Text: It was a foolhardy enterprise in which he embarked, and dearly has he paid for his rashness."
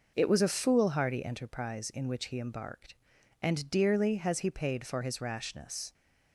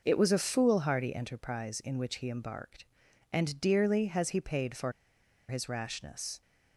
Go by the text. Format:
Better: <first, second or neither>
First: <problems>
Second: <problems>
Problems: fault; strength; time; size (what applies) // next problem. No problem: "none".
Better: first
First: none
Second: pauses between "for" and "his"; noticeable; at 4.9 s; 0.56 s long